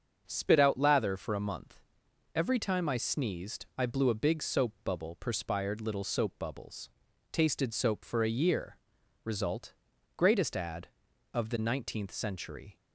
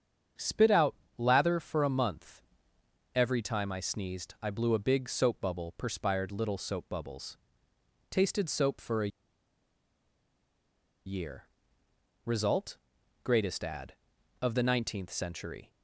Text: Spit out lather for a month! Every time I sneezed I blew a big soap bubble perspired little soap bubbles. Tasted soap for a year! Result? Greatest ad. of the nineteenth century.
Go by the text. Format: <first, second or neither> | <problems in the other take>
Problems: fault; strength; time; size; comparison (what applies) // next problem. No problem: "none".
first | starts louder than the rest; strong; until 1.6 s; 7.5 dB; also in the first // pauses between "out" and "lather"; slight; at 0.9 s; 0.22 s long // pauses between "a" and "year"; strong; at 9.0 s; 1.9 s long